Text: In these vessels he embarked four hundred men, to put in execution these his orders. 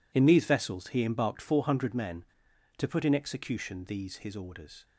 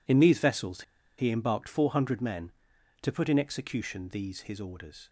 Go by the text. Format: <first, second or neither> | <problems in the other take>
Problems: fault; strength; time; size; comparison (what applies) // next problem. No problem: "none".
first | pauses between "vessels" and "he"; slight; at 0.8 s; 0.36 s long